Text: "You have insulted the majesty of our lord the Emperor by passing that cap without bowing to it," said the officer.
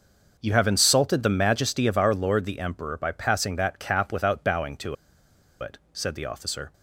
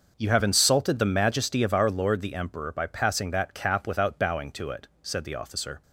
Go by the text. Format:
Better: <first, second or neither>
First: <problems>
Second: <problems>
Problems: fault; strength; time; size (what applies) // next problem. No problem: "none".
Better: second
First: pauses between "to" and "it"; noticeable; at 4.9 s; 0.65 s long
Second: none